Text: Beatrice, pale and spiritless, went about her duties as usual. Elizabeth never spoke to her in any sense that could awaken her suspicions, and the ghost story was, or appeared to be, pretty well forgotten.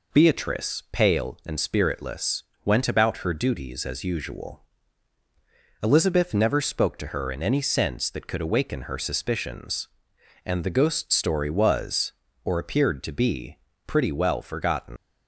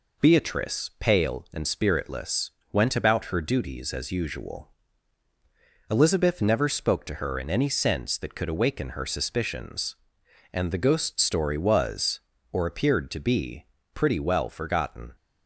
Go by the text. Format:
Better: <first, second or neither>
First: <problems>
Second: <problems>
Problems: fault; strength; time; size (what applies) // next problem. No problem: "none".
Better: second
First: leaves "forgotten" unfinished; at 14.9 s; 115 ms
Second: none